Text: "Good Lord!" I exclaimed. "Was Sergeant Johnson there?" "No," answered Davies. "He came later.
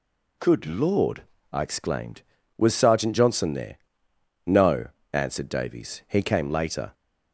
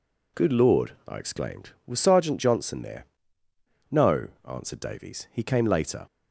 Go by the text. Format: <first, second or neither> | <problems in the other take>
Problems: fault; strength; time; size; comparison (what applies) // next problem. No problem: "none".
neither | none